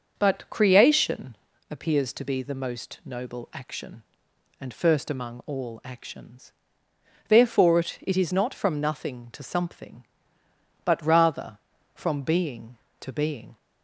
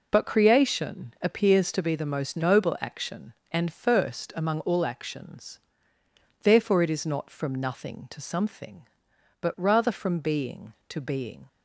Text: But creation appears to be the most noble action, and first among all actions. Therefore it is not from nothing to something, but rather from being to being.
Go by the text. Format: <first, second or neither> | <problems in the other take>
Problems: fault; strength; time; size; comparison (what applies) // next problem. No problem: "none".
second | starts louder than the rest; until 1.1 s; 6 dB // pauses between "creation" and "appears"; slight; at 1.3 s; 0.34 s long // says "it" twice; at 8.0 s